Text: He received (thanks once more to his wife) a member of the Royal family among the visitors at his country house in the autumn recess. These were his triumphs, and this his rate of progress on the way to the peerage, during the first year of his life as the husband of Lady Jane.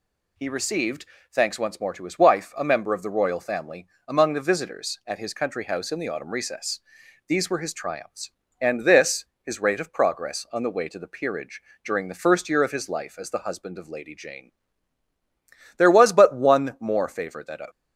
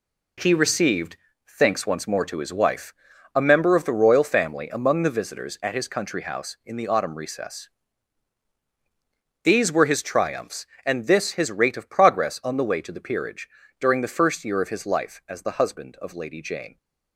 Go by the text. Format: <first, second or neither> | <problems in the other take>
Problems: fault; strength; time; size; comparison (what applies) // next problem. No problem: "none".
second | pauses between "family" and "among"; slight; at 3.8 s; 0.20 s long // pauses between "this" and "his"; slight; at 9.2 s; 0.16 s long // goes on to say "There was but one more favor that"; strong; from 15.7 s on; 1.8 s long